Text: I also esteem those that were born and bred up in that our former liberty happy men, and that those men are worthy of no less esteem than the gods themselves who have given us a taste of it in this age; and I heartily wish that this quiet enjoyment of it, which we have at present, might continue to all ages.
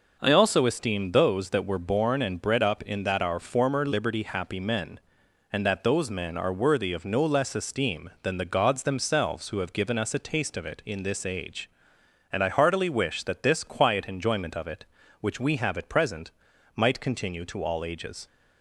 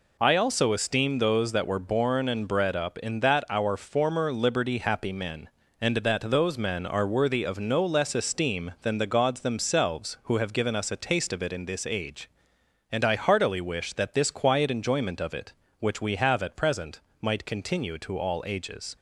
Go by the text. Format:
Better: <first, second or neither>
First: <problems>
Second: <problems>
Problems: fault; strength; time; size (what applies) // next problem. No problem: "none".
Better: neither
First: none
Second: none